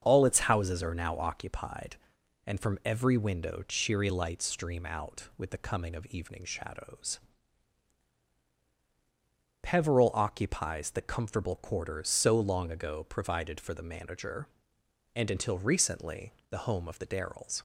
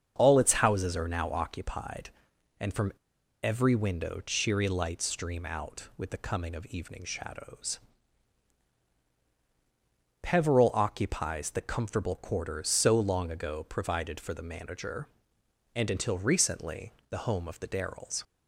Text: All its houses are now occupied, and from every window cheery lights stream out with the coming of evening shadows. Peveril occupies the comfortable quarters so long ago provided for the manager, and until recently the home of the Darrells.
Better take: first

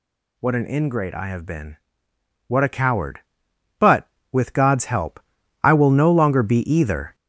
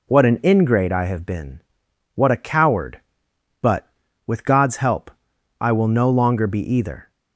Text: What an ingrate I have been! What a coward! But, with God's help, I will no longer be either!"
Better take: second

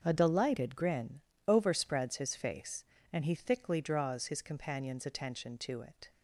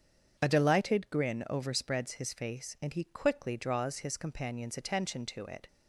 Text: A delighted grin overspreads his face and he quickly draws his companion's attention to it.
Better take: second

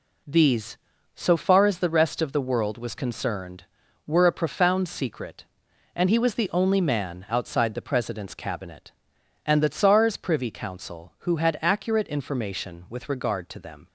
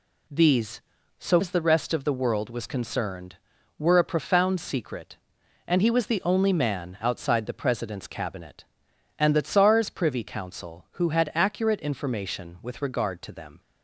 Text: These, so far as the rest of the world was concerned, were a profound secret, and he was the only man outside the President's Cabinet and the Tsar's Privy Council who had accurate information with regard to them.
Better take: first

